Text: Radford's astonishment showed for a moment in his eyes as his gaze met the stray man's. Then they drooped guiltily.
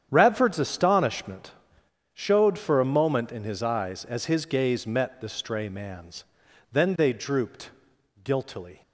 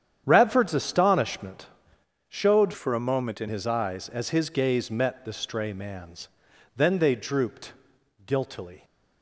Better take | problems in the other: first | starts louder than the rest; strong; until 1.2 s; 9 dB; strong in the first // pauses between "astonishment" and "showed"; noticeable; at 1.6 s; 0.62 s long; noticeable in the first // changes voice from "for" to "in"; from 2.7 to 3.4 s; 0.7 s long // pauses between "drooped" and "guiltily"; noticeable; at 7.7 s; 0.54 s long; noticeable in the first

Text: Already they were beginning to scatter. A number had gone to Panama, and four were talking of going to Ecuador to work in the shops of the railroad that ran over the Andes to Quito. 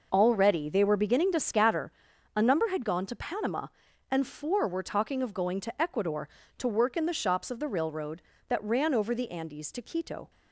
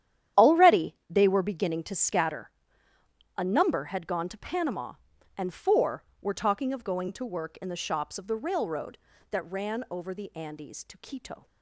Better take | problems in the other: first | starts louder than the rest; strong; until 1.4 s; 10.5 dB // skips "to Ecuador"; at 7.1 s

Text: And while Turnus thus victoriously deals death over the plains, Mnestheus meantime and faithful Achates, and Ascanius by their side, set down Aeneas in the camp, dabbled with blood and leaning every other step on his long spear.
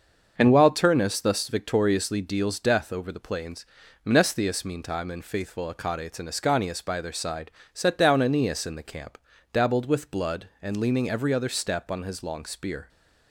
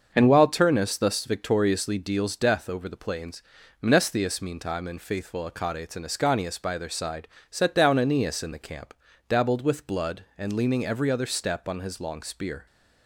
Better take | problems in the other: neither | starts louder than the rest; the same in both

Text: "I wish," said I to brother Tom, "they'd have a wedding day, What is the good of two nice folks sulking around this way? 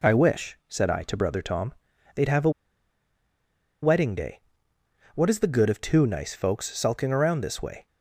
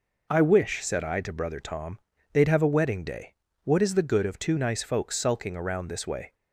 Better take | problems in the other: second | pauses between "a" and "wedding"; strong; at 2.5 s; 1.3 s long

